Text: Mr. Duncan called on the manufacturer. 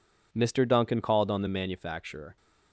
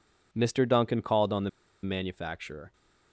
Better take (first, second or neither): first